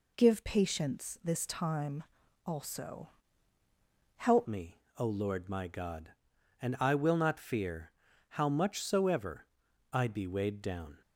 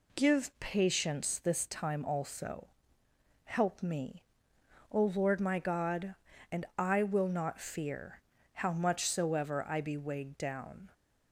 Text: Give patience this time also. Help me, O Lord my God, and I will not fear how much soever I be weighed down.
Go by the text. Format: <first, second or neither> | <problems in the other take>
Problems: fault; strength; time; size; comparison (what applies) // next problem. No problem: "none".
second | pauses between "time" and "also"; at 2.0 s; 0.42 s long // changes voice at "me"; from 4.4 s on; 6.6 s long // pauses between "fear" and "how"; at 7.9 s; 0.38 s long; slight in the second // pauses between "soever" and "I"; noticeable; at 9.4 s; 0.46 s long